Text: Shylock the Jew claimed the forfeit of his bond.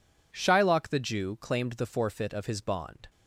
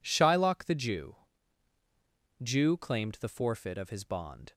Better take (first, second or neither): first